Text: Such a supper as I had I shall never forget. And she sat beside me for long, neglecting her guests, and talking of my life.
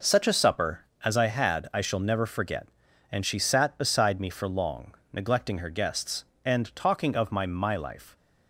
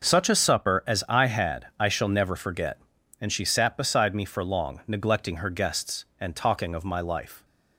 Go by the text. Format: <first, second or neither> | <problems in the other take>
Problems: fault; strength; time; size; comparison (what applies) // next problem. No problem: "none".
second | says "my" twice; at 7.4 s